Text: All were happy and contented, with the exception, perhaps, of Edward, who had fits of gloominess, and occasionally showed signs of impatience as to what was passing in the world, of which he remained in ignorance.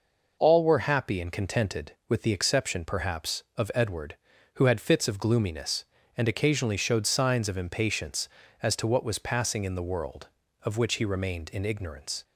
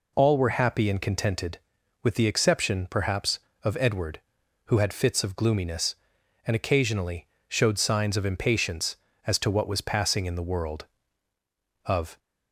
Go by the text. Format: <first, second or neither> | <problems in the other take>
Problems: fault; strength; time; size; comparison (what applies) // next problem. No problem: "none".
first | pauses between "occasionally" and "showed"; slight; at 7.2 s; 0.22 s long // stops before "which he remained in ignorance"; at 12.1 s